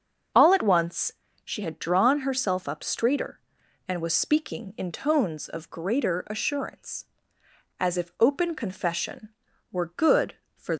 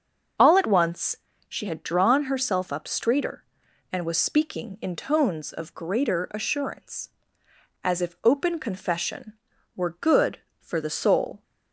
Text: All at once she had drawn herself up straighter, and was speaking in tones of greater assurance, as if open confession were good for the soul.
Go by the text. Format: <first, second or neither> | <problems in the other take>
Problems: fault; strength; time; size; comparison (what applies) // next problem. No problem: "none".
second | starts louder than the rest; until 1.6 s; 7 dB; also in the second // pauses between "once" and "she"; slight; at 1.1 s; 0.32 s long; slight in the second // stops before "the soul"; at 10.7 s